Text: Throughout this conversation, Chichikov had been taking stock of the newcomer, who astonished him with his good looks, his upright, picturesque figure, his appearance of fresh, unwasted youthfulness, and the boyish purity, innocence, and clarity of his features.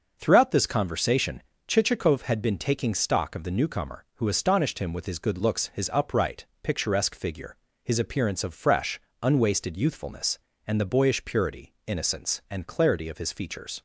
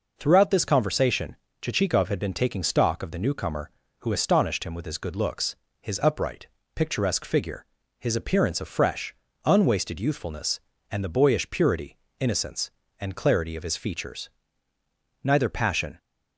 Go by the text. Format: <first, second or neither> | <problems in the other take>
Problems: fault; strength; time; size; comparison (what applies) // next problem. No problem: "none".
first | goes on to say "Neither passion"; noticeable; from 15.2 s on; 0.76 s long